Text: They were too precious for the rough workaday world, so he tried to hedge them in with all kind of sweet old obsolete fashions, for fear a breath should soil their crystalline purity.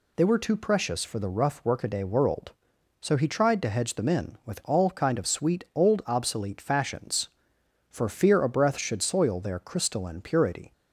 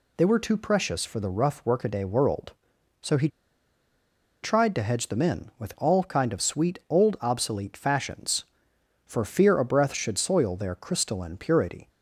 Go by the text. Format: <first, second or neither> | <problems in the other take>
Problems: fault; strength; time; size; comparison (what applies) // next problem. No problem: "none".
first | pauses between "he" and "tried"; at 3.2 s; 1.1 s long